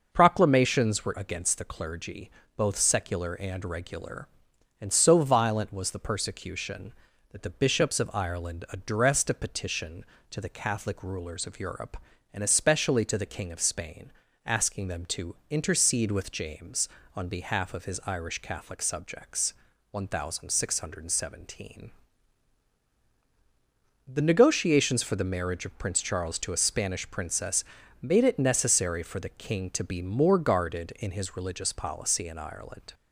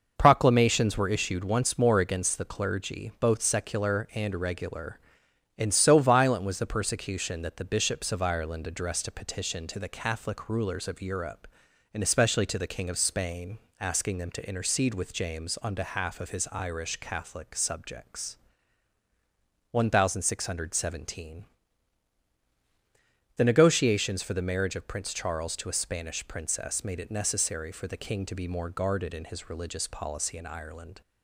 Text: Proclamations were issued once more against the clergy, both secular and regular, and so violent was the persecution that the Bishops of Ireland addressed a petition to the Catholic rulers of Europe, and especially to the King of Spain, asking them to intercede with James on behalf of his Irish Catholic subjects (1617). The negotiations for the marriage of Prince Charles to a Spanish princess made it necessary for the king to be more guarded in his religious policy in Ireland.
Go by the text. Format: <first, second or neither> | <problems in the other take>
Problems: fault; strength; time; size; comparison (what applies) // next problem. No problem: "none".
second | skips "issued once more"; at 1.1 s // pauses between "to" and "intercede"; slight; at 15.3 s; 0.16 s long // pauses between "princess" and "made"; at 27.6 s; 0.40 s long